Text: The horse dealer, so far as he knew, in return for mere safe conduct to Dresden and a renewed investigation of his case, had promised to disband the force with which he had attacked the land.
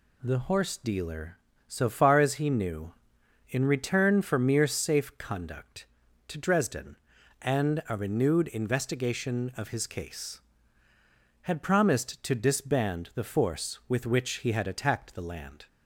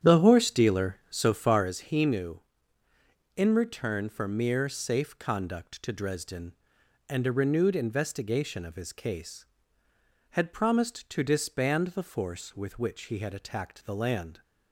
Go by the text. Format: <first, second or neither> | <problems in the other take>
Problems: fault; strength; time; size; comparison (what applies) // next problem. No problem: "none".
first | starts louder than the rest; strong; until 1.8 s; 9 dB